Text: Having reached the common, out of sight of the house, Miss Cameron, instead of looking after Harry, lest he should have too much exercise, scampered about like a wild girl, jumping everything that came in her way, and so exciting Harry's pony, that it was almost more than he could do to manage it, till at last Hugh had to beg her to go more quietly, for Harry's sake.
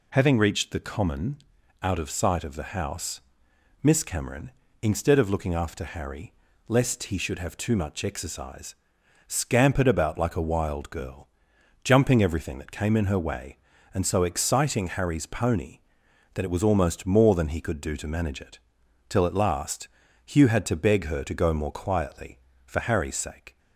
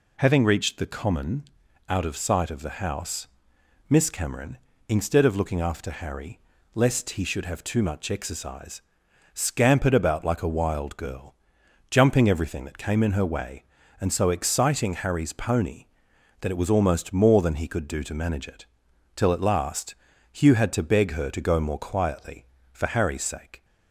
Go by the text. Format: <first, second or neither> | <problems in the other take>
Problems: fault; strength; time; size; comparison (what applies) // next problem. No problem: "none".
neither | pauses between "last" and "Hugh"; slight; the same in both